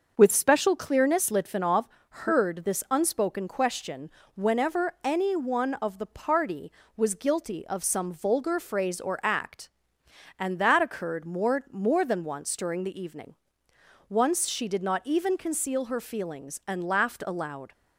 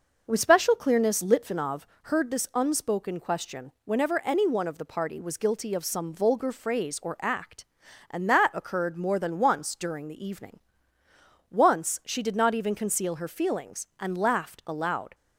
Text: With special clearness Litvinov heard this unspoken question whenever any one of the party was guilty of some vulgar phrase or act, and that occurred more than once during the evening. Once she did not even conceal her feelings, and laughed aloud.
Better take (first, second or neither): second